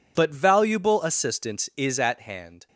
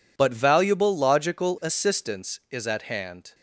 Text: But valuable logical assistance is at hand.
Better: second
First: skips "logical"; at 1.0 s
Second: none

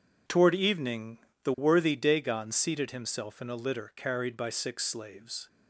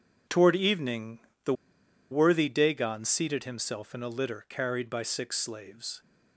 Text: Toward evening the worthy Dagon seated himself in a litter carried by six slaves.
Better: first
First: pauses between "evening" and "the"; slight; at 1.1 s; 0.26 s long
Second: pauses between "evening" and "the"; slight; at 1.1 s; 0.26 s long // pauses between "the" and "worthy"; noticeable; at 1.5 s; 0.58 s long

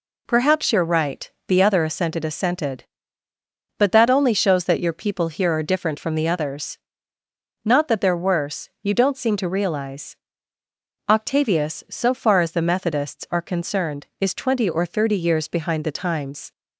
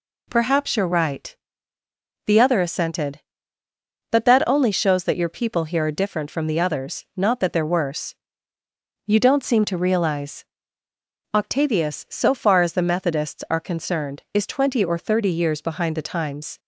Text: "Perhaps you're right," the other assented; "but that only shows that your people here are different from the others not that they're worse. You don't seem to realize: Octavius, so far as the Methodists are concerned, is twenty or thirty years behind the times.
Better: second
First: says "assented" twice; at 2.2 s // pauses between "others" and "not"; noticeable; at 6.7 s; 0.88 s long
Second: none

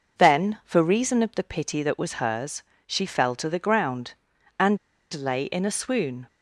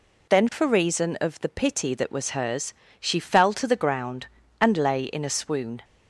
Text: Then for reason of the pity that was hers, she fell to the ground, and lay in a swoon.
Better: second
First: pauses between "and" and "lay"; slight; at 4.7 s; 0.35 s long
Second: none

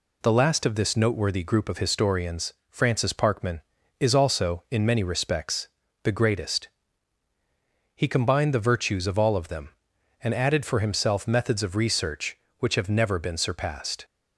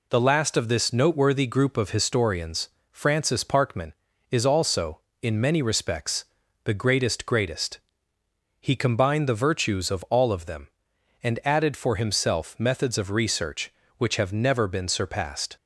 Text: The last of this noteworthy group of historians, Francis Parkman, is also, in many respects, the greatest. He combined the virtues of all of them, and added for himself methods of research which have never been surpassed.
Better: first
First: none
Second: says "greatest" twice; at 7.2 s

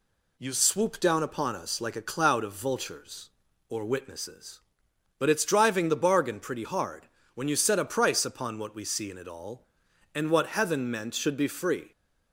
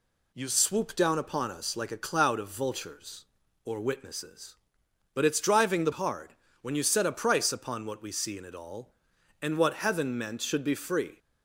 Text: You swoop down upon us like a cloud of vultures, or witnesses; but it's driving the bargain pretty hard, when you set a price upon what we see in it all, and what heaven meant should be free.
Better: first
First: none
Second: skips "bargain pretty"; at 5.9 s

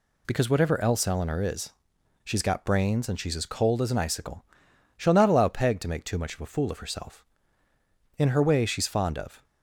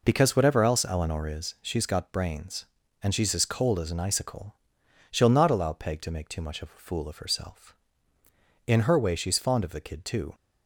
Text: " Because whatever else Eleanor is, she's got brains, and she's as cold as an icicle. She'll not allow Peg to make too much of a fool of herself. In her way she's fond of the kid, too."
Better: second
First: stops before "the kid too"; at 9.4 s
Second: none

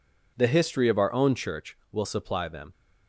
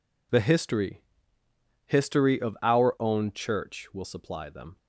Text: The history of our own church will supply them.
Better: first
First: none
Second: says "history" twice; at 1.8 s

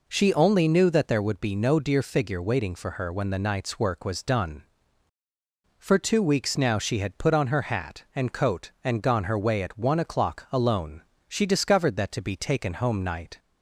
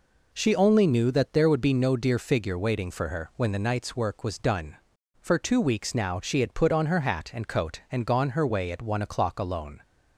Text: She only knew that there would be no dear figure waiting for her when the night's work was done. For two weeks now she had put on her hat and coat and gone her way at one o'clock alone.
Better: second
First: goes on to say "She discovered that to be taken home night"; strong; from 11.2 s on; 2.1 s long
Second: none

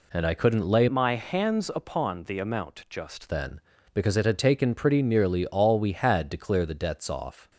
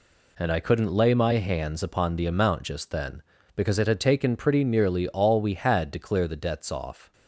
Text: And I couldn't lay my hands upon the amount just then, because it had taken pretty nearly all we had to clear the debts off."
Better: second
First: changes voice from "my" to "just"; from 0.8 to 3.3 s; 2.5 s long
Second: none

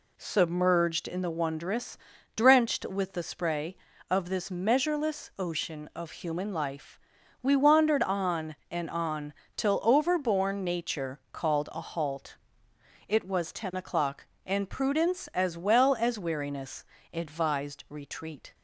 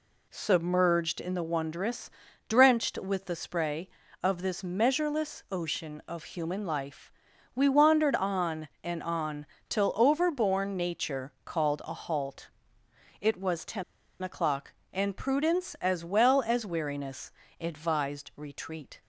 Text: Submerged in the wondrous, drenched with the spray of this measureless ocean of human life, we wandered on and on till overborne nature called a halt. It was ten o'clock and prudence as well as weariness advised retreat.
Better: first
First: pauses between "on" and "till"; slight; at 9.3 s; 0.24 s long // pauses between "weariness" and "advised"; slight; at 16.8 s; 0.30 s long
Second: pauses between "on" and "till"; slight; at 9.4 s; 0.24 s long // pauses between "ten" and "o'clock"; at 13.8 s; 0.39 s long // pauses between "weariness" and "advised"; slight; at 17.3 s; 0.30 s long

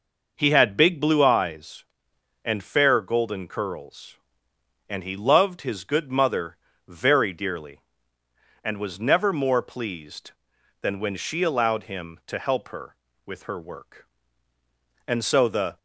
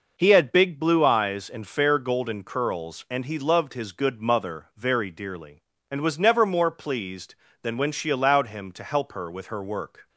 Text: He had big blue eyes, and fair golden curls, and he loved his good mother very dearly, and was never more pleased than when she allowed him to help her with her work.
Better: second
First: pauses between "mother" and "very"; slight; at 6.5 s; 0.28 s long // goes on to say "And so the"; noticeable; from 15.0 s on; 0.70 s long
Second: none

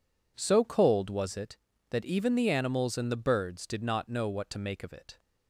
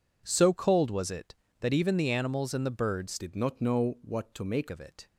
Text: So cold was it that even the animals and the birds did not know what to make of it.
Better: first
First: none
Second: changes voice from "did" to "make"; from 3.1 to 4.6 s; 1.5 s long

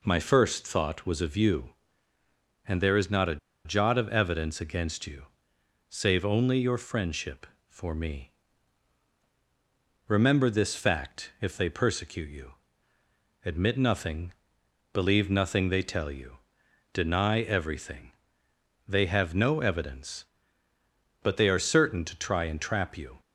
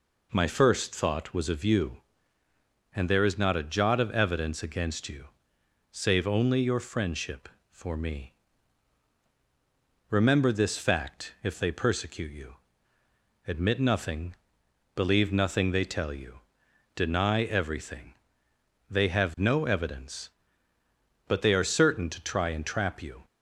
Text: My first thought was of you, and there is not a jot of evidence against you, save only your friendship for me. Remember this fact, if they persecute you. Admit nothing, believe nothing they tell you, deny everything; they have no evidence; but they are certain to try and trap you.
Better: second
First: pauses between "a" and "jot"; slight; at 3.3 s; 0.28 s long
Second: none

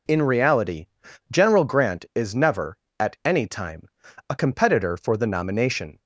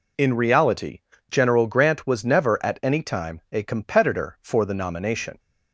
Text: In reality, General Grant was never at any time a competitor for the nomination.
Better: second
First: says "is" for "was"; at 2.1 s // pauses between "time" and "a"; at 3.8 s; 0.40 s long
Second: none

